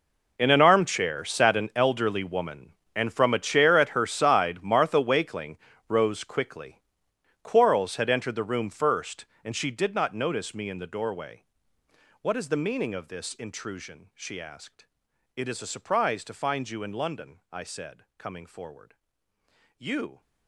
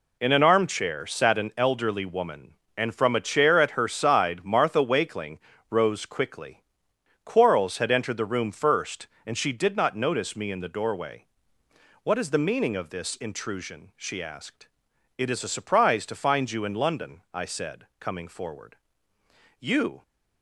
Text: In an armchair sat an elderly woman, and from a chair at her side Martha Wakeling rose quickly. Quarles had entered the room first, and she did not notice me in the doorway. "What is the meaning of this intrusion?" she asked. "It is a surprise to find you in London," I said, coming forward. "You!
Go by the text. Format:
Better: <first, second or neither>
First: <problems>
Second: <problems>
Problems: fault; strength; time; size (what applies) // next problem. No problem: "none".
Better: second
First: gets quieter; strong; throughout; 17.5 dB // pauses between "Wakeling" and "rose"; slight; at 5.5 s; 0.32 s long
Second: pauses between "Wakeling" and "rose"; slight; at 5.3 s; 0.32 s long